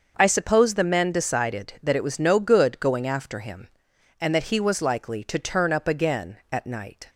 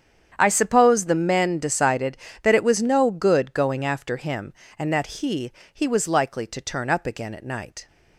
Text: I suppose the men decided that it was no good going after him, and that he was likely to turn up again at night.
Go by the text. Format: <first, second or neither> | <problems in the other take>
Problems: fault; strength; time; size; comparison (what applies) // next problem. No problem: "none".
first | starts louder than the rest; strong; until 1.3 s; 8.5 dB; also in the first // says "he" twice; at 5.7 s